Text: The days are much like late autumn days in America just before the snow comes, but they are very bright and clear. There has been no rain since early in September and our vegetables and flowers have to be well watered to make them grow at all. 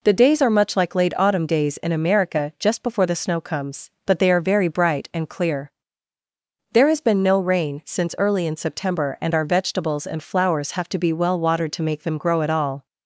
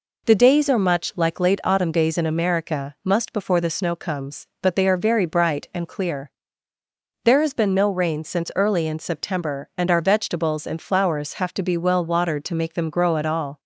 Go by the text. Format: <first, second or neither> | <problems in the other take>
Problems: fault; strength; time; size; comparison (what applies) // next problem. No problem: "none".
first | says "must" for "just"; at 3.0 s